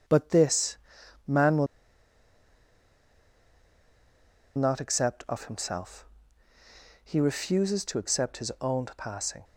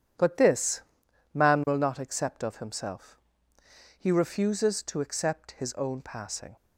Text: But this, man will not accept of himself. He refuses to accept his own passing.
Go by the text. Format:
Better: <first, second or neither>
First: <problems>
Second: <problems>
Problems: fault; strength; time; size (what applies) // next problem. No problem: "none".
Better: second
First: pauses between "will" and "not"; strong; at 1.6 s; 2.8 s long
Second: none